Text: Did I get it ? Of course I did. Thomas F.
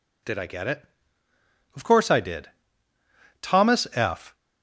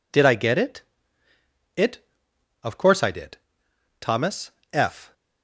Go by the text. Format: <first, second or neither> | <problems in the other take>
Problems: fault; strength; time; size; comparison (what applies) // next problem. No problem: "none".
first | says "it" twice; at 1.7 s // pauses between "Thomas" and "F"; slight; at 4.4 s; 0.24 s long